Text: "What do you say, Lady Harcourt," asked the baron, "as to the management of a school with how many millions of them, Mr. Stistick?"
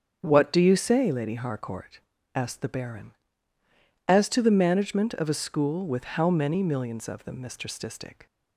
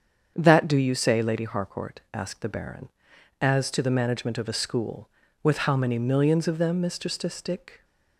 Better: first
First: starts louder than the rest; strong; until 1.2 s; 7.5 dB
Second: starts louder than the rest; strong; until 1.3 s; 7.5 dB // says "That" for "What"; at 0.3 s

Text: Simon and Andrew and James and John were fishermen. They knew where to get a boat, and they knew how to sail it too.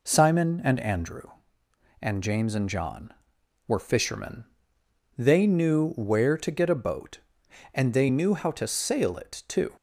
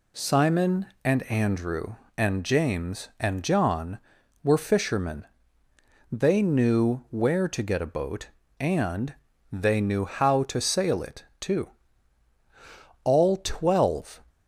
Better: first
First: none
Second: pauses between "and" and "they"; at 9.1 s; 0.38 s long // pauses between "it" and "too"; slight; at 11.2 s; 0.16 s long // goes on to say "All twelve"; noticeable; from 13.0 s on; 1.2 s long

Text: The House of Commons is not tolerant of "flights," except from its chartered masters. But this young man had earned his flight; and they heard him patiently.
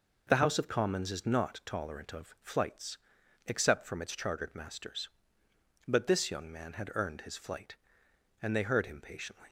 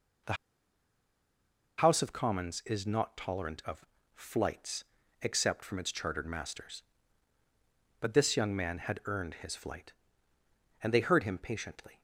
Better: first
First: none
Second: pauses between "The" and "House"; strong; at 0.3 s; 1.4 s long // pauses between "of" and "flights"; slight; at 3.8 s; 0.30 s long

